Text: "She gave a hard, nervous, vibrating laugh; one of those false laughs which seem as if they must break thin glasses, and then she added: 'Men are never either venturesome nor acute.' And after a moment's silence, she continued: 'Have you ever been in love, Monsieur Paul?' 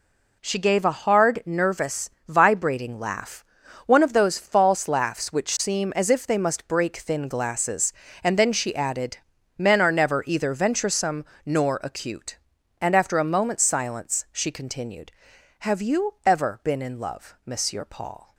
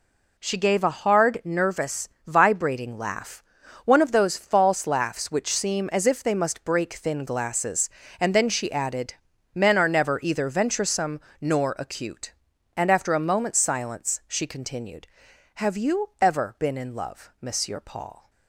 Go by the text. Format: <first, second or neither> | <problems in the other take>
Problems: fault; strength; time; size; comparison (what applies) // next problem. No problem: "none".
neither | pauses between "venturesome" and "nor"; slight; the same in both